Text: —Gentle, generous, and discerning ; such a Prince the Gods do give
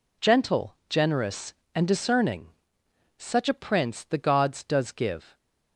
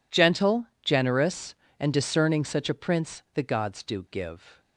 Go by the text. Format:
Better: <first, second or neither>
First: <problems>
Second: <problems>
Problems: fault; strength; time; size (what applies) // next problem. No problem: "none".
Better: second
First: says "does" for "do"; at 4.6 s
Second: none